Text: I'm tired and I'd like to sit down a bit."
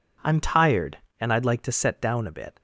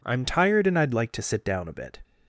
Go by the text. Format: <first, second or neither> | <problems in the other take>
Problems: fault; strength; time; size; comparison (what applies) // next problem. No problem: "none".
second | says "set" for "sit"; at 1.7 s